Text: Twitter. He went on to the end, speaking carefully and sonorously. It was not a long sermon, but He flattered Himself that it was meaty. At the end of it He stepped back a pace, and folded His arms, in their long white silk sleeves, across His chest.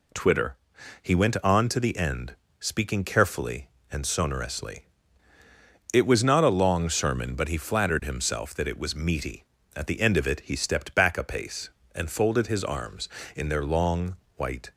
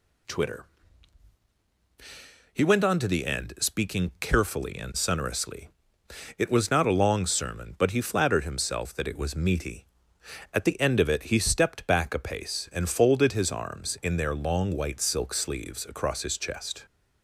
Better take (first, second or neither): second